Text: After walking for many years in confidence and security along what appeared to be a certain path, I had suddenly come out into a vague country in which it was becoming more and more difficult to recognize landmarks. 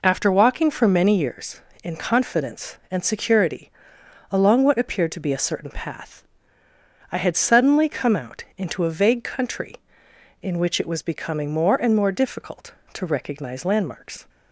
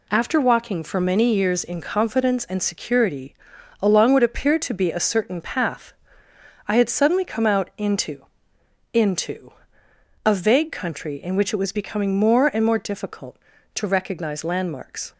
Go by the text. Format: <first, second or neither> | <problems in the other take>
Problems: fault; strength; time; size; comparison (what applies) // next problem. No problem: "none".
first | pauses between "security" and "along"; noticeable; at 3.3 s; 0.48 s long; noticeable in the first // says "into" twice; at 8.9 s